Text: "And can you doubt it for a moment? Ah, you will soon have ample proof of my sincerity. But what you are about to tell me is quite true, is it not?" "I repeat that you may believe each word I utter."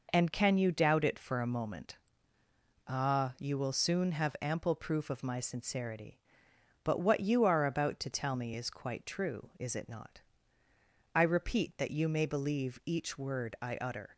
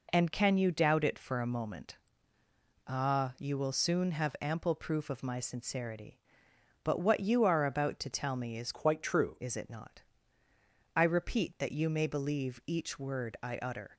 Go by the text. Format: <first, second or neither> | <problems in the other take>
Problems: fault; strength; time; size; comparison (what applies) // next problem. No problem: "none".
first | changes voice from "quite" to "true"; from 8.7 to 9.3 s; 0.6 s long